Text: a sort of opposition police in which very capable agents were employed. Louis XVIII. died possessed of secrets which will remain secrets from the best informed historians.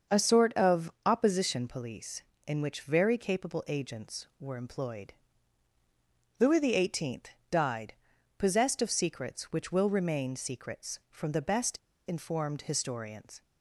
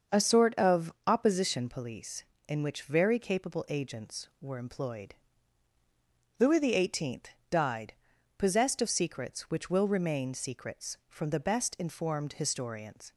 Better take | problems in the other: second | starts louder than the rest; until 1.2 s; 6.5 dB; also in the second // pauses between "died" and "possessed"; at 7.9 s; 0.44 s long; also in the second // pauses between "best" and "informed"; slight; at 11.7 s; 0.32 s long

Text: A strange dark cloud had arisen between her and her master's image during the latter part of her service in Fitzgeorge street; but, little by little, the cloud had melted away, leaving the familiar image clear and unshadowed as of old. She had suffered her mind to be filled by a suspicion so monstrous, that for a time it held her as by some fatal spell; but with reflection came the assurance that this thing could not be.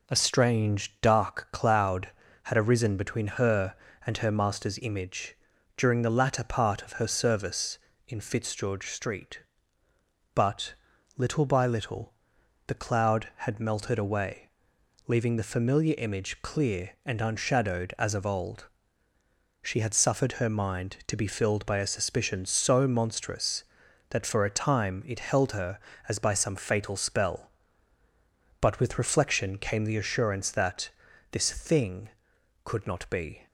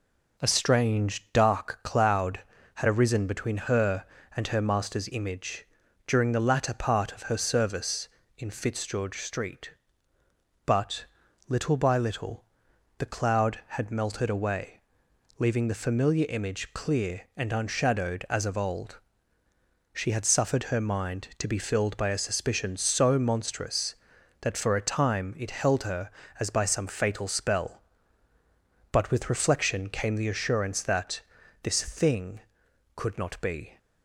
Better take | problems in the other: neither | pauses between "image" and "during"; the same in both // pauses between "that" and "this"; the same in both

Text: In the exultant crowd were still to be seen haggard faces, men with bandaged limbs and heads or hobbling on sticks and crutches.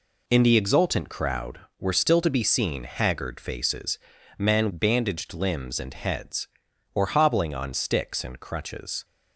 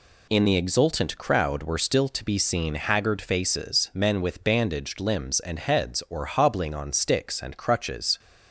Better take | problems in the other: second | skips "with"; at 4.7 s

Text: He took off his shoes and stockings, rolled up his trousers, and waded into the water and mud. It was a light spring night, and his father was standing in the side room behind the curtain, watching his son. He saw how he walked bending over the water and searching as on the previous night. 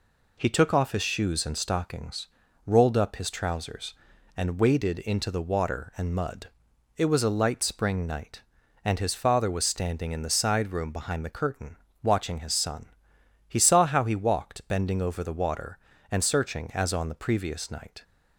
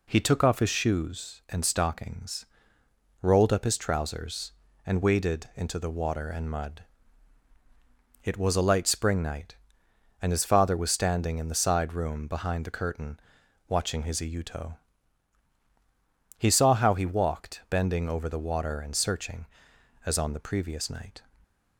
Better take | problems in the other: first | says "iuto" for "son"; at 14.2 s

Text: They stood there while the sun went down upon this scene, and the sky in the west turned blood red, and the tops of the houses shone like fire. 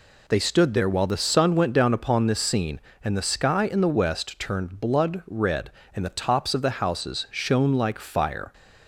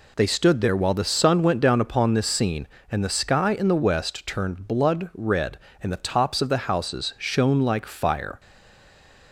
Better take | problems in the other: first | stays silent after the last word; slight; from 8.3 s on; 1.0 s long

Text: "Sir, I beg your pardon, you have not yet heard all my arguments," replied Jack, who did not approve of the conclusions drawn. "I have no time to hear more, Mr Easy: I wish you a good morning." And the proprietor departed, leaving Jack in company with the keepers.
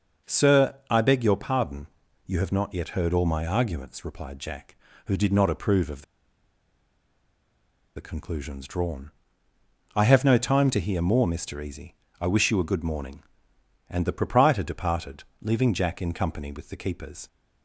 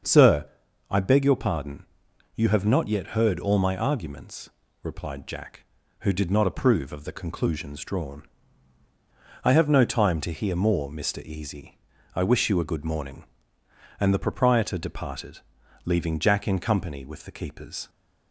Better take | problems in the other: second | starts louder than the rest; noticeable; until 1.3 s; 6 dB; also in the second // pauses between "of" and "the"; strong; at 6.0 s; 1.9 s long

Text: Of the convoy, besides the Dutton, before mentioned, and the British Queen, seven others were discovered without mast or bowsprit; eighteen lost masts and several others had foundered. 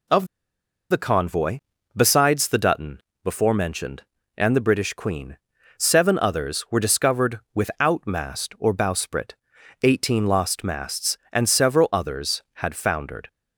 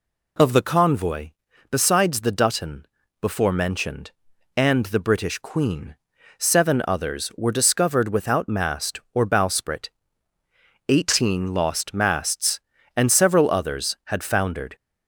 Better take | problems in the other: second | pauses between "Of" and "the"; noticeable; at 0.2 s; 0.66 s long

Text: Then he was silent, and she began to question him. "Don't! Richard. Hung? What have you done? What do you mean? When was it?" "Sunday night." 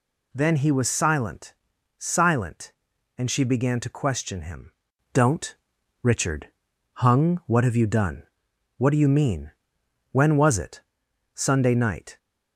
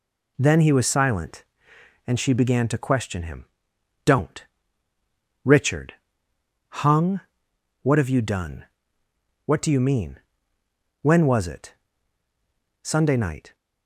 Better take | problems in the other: second | says "silent" twice; at 2.0 s

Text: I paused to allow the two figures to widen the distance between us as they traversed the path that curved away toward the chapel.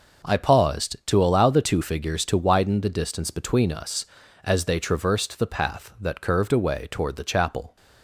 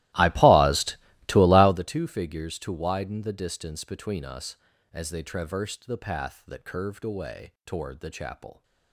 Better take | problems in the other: first | starts louder than the rest; strong; until 1.9 s; 17 dB

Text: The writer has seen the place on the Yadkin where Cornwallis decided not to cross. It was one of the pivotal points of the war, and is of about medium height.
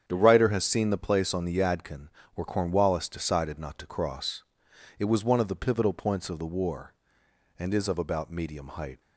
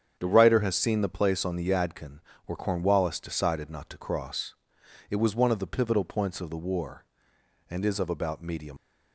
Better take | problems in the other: first | starts louder than the rest; strong; until 1.2 s; 8 dB; strong in the first // pauses between "Yadkin" and "where"; slight; at 2.1 s; 0.28 s long; slight in the first // stops before "height"; at 8.7 s

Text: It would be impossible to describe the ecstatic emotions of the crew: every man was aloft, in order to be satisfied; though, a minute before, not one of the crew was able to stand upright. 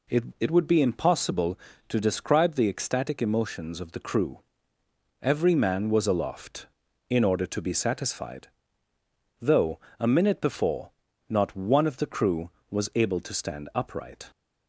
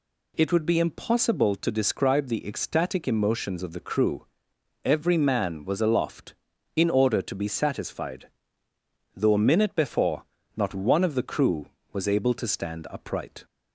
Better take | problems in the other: second | says "It" twice; at 0.4 s

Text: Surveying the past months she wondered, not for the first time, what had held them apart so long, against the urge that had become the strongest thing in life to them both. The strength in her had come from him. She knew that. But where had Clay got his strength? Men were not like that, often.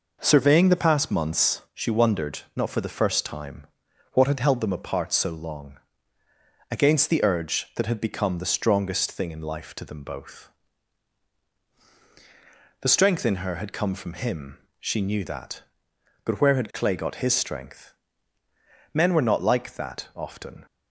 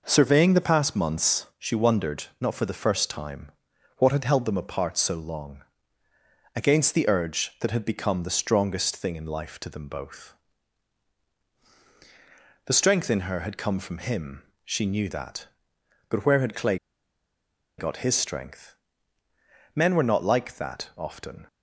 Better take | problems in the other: first | pauses between "Clay" and "got"; at 16.7 s; 1.0 s long

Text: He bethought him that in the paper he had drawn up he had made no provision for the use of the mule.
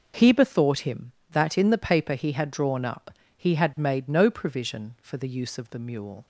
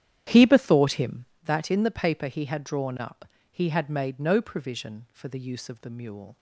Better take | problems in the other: first | starts louder than the rest; strong; until 1.5 s; 10 dB // pauses between "up" and "he"; slight; at 3.2 s; 0.24 s long; slight in the first

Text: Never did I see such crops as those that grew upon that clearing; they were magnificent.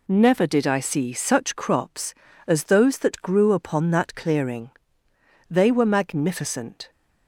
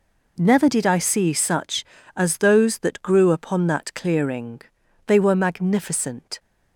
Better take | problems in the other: first | skips "crops"; at 1.9 s

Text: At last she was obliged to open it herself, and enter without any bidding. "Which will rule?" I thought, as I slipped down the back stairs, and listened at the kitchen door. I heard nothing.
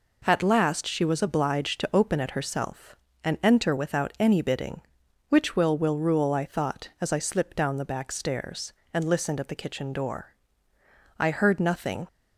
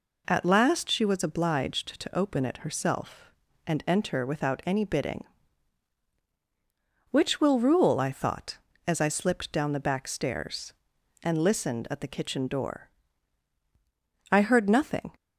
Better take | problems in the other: second | says "will" twice; at 5.7 s

